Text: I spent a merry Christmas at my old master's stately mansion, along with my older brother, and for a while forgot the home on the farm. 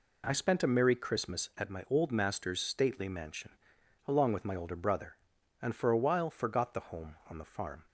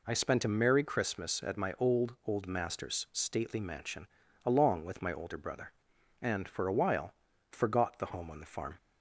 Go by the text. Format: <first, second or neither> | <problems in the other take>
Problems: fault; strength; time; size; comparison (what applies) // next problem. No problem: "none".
first | says "old" twice; at 2.2 s // pauses between "while" and "forgot"; at 7.1 s; 0.38 s long